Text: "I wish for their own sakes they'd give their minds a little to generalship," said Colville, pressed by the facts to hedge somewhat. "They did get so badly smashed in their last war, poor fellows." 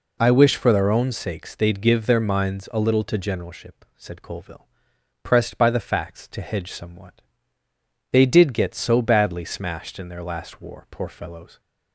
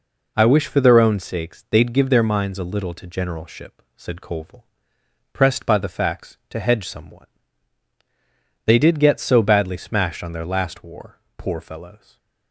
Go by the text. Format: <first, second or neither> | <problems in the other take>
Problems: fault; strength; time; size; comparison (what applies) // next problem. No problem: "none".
first | says "on" for "in"; at 10.2 s // stays silent after the last word; slight; from 11.9 s on; 0.6 s long